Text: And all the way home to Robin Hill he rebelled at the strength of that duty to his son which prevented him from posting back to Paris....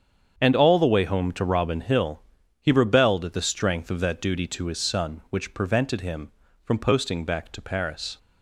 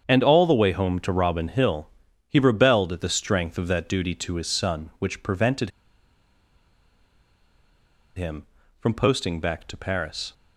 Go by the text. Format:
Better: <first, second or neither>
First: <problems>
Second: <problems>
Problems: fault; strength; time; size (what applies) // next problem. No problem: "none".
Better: first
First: starts louder than the rest; strong; until 1.3 s; 7.5 dB // pauses between "Hill" and "he"; at 2.2 s; 0.38 s long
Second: starts louder than the rest; strong; until 1.0 s; 7.5 dB // pauses between "Hill" and "he"; at 1.8 s; 0.38 s long // pauses between "prevented" and "him"; strong; at 5.6 s; 2.4 s long